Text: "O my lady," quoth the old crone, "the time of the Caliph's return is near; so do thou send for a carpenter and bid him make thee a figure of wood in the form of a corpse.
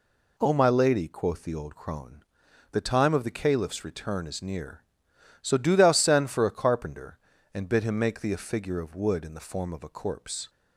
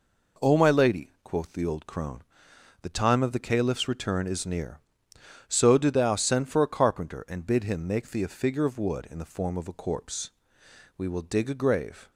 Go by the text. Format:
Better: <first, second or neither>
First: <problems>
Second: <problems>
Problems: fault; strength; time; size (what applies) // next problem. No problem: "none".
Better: first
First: none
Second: goes on to say "We will dig a grave"; noticeable; from 10.9 s on; 1.1 s long